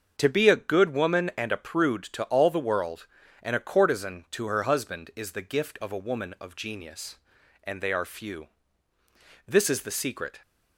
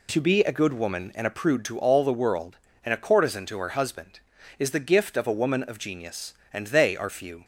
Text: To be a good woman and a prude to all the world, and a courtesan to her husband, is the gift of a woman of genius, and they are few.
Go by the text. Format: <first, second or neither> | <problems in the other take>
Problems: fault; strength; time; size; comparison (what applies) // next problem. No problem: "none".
second | starts louder than the rest; until 1.1 s; 7 dB // goes on to say "This is the secret"; noticeable; from 9.4 s on; 0.96 s long